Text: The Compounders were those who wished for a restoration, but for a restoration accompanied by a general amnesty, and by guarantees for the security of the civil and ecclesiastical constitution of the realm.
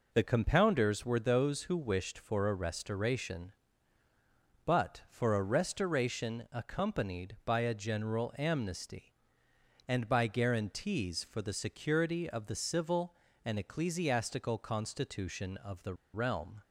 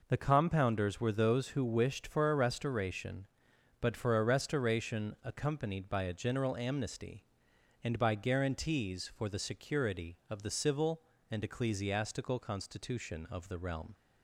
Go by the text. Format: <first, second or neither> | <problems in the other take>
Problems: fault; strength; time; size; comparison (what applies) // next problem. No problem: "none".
second | pauses between "the" and "realm"; slight; at 15.9 s; 0.20 s long